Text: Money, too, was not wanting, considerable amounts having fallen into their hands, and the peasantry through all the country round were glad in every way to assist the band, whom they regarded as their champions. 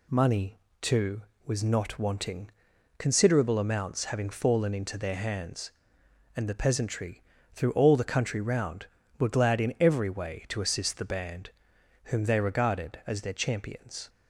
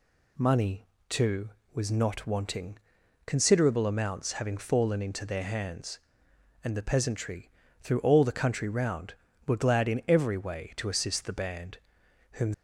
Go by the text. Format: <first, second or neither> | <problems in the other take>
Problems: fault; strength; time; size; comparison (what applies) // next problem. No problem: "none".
first | pauses between "peasantry" and "through"; slight; at 7.4 s; 0.32 s long; slight in the first // stops before "they regarded as their champions"; at 12.5 s